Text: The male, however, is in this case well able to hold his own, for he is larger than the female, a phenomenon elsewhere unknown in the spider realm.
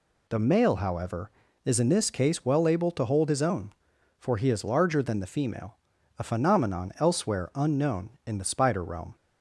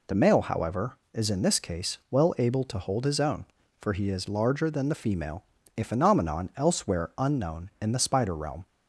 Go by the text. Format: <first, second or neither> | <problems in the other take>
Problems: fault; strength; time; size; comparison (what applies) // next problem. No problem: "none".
neither | none